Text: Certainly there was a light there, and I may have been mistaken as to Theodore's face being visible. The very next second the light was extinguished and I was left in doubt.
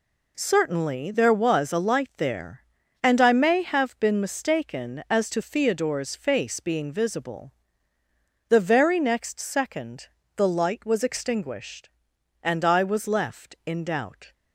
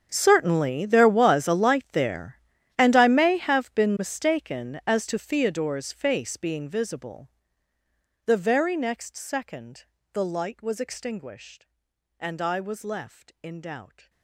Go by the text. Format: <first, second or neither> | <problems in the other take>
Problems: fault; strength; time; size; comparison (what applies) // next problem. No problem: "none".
first | gets quieter; strong; throughout; 19.5 dB // pauses between "second" and "the"; slight; at 9.8 s; 0.28 s long; slight in the first